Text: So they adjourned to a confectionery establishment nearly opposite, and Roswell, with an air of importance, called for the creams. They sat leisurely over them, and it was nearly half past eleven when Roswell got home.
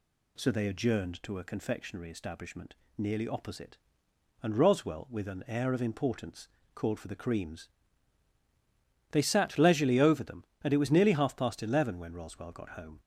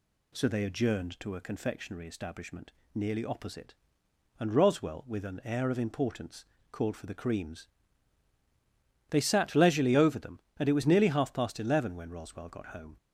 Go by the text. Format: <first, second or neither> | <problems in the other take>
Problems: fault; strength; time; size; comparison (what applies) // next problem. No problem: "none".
neither | pauses between "establishment" and "nearly"; slight; the same in both